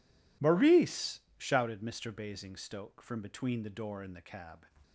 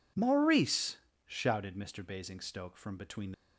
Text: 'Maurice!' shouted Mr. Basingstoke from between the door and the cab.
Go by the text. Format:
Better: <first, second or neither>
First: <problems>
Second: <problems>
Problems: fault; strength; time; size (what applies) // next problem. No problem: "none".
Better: first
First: none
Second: stops before "the door and the cab"; at 3.3 s